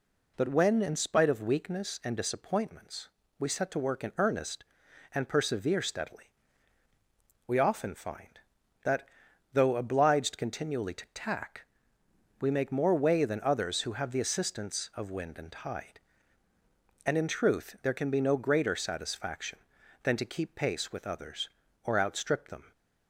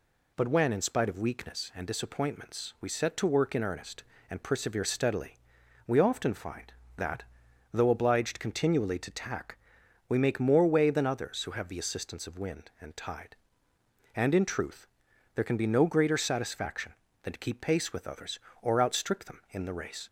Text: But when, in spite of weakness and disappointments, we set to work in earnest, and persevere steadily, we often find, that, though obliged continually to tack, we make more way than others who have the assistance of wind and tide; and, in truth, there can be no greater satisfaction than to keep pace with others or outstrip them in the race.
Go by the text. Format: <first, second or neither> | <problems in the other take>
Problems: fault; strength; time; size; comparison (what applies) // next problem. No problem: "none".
second | stops before "in the race"; at 22.7 s